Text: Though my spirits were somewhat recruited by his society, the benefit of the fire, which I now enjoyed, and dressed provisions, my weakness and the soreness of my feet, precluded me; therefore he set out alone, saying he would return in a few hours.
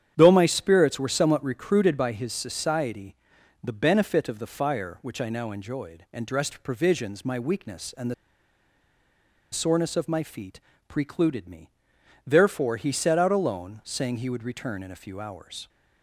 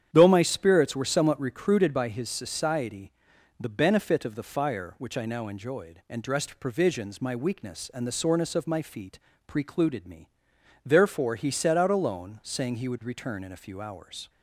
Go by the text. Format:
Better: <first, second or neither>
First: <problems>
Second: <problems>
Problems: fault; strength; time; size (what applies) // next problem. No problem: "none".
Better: second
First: starts louder than the rest; strong; until 1.1 s; 9 dB // pauses between "the" and "soreness"; strong; at 8.1 s; 1.3 s long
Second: starts louder than the rest; strong; until 1.1 s; 9 dB